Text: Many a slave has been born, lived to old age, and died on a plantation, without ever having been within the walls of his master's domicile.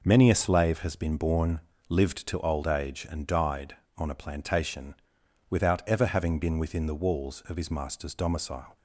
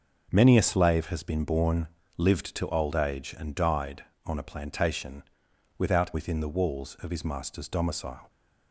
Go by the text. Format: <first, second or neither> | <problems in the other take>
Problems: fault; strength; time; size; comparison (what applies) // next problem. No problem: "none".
first | starts louder than the rest; noticeable; until 1.3 s; 6 dB // skips "ever having been"; at 6.1 s